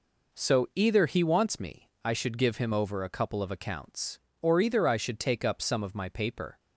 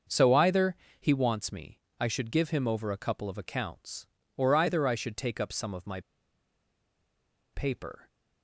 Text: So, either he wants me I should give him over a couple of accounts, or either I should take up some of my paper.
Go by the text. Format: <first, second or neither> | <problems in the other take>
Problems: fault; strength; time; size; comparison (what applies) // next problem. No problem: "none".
first | pauses between "either" and "he"; slight; at 0.7 s; 0.26 s long // pauses between "me" and "I"; slight; at 1.7 s; 0.20 s long; slight in the first // pauses between "my" and "paper"; strong; at 5.9 s; 1.5 s long